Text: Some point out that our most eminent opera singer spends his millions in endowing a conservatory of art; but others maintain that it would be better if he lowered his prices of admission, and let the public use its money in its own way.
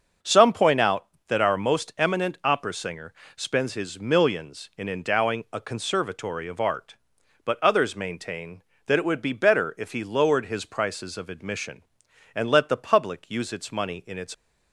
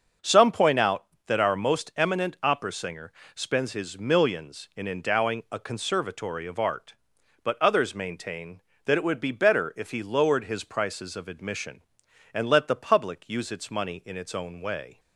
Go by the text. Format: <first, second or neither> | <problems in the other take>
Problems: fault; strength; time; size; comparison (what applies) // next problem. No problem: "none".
second | starts louder than the rest; until 1.4 s; 6.5 dB; also in the second // pauses between "singer" and "spends"; slight; at 3.1 s; 0.22 s long; slight in the second // stops before "own way"; at 14.3 s